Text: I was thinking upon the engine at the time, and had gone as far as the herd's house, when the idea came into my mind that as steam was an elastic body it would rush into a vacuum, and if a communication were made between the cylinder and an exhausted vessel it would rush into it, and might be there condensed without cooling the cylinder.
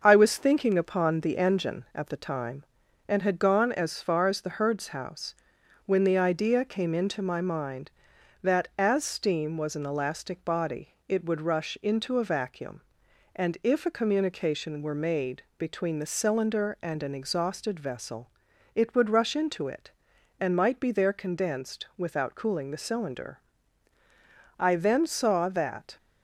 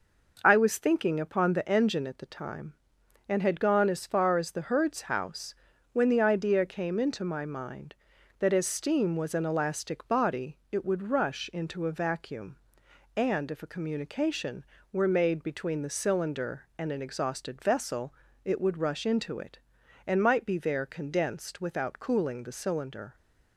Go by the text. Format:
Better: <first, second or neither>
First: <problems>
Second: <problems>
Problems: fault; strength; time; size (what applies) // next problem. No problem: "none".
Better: second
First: starts louder than the rest; until 1.0 s; 6.5 dB // pauses between "vessel" and "it"; noticeable; at 18.2 s; 0.46 s long // goes on to say "I then saw that"; from 24.5 s on; 1.3 s long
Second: pauses between "vessel" and "it"; slight; at 18.1 s; 0.30 s long